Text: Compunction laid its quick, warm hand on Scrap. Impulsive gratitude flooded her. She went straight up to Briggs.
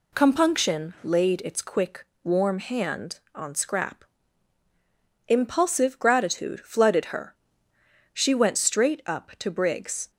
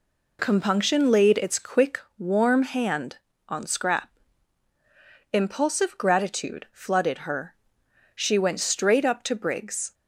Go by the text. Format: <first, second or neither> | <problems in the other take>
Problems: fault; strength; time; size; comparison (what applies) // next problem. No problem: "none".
neither | none